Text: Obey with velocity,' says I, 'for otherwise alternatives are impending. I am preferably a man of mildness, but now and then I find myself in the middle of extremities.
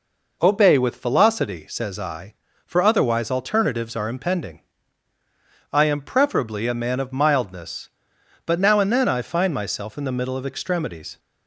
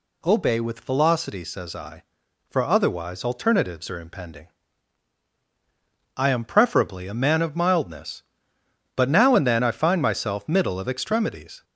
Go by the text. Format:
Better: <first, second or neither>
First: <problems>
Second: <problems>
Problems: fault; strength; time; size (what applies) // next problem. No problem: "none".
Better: first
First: none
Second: skips "in the"; at 10.4 s